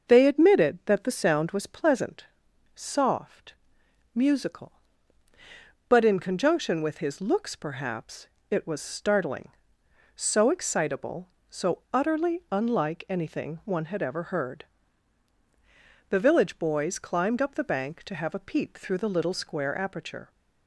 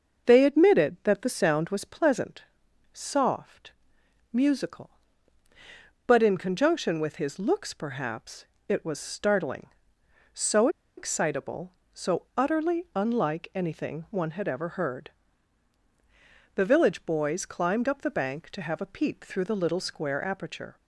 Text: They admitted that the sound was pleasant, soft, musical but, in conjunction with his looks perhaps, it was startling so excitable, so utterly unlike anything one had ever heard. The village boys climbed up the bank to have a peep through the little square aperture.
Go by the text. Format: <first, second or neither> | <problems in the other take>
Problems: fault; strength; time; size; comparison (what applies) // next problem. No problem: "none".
first | starts louder than the rest; until 1.3 s; 6.5 dB; also in the first // pauses between "so" and "excitable"; slight; at 10.6 s; 0.28 s long